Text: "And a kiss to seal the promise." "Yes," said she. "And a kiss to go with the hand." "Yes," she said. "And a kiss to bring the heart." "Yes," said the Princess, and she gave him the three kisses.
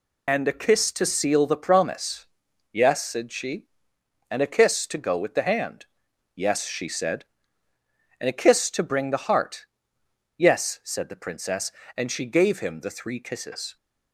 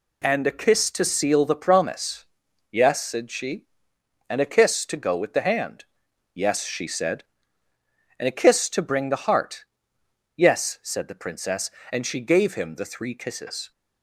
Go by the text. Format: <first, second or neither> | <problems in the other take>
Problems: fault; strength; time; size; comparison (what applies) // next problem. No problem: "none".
second | loses the start of "And"; at 0.2 s; 50 ms